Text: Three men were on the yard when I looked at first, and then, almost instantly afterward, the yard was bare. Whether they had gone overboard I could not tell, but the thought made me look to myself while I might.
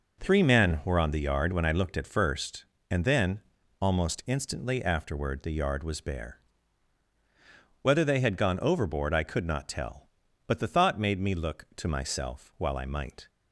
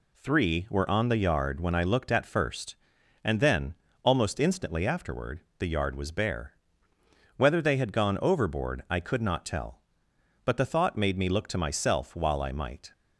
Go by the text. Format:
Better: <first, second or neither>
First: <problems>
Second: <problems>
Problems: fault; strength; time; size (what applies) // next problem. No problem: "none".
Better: first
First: none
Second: skips "men"; at 0.6 s